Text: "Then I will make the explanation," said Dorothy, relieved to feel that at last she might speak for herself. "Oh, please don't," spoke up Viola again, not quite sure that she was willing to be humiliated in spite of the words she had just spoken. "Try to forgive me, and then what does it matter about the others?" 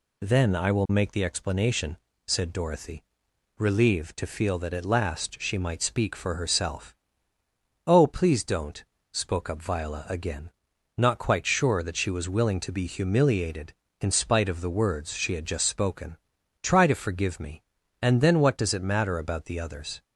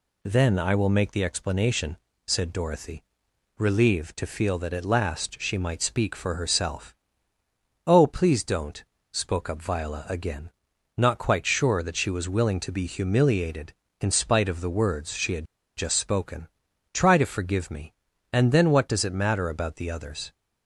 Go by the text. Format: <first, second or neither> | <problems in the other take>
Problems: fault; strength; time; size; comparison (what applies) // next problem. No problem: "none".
first | pauses between "had" and "just"; slight; at 15.4 s; 0.31 s long